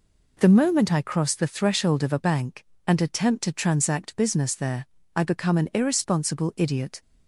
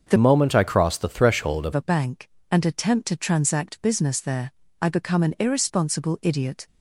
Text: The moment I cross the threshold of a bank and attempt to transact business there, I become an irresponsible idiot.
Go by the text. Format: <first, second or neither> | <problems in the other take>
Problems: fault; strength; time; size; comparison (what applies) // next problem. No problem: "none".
first | starts louder than the rest; until 1.1 s; 6.5 dB // changes voice from "moment" to "of"; from 0.1 to 1.7 s; 1.6 s long